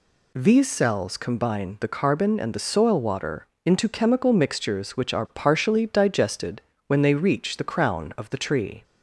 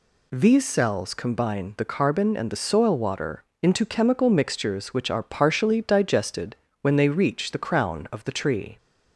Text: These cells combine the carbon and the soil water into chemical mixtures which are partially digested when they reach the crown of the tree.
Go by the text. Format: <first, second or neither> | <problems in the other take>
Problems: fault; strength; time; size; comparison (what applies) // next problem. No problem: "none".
neither | pauses between "water" and "into"; slight; the same in both // pauses between "digested" and "when"; slight; the same in both